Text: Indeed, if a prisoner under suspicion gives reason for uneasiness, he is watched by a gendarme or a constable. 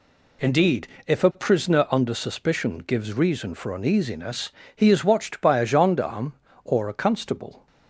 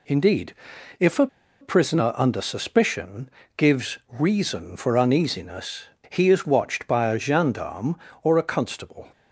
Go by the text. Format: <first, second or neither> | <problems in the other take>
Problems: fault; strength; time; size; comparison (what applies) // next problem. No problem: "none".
first | pauses between "a" and "prisoner"; slight; at 1.2 s; 0.34 s long // pauses between "suspicion" and "gives"; slight; at 3.2 s; 0.26 s long